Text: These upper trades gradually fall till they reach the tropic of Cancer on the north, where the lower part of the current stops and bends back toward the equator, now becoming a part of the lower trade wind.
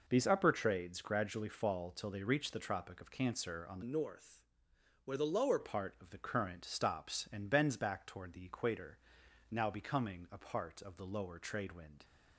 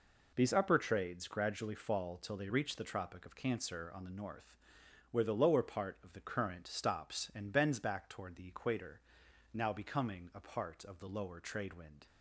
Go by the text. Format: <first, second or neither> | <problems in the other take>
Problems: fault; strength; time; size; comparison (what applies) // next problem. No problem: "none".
second | changes voice from "north" to "lower"; from 3.8 to 5.5 s; 1.7 s long